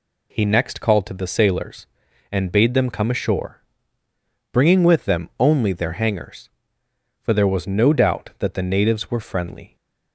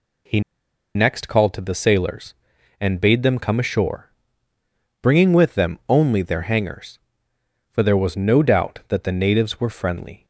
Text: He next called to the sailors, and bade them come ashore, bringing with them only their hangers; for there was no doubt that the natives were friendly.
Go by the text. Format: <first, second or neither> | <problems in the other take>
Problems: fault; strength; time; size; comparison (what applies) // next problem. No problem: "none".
first | pauses between "He" and "next"; noticeable; at 0.4 s; 0.54 s long